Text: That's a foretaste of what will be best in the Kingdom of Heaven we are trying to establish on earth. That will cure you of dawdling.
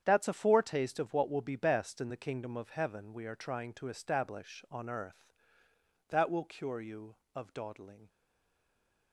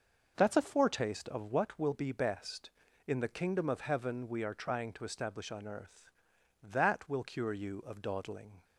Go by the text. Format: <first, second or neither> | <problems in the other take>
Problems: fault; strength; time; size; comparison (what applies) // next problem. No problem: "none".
second | starts louder than the rest; strong; until 1.0 s; 8.5 dB; noticeable in the second // stays silent after the last word; from 8.0 s on; 1.1 s long